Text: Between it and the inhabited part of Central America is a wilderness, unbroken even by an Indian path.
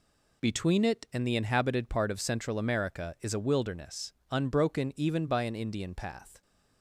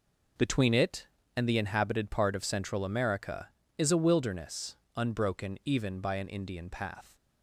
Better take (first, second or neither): neither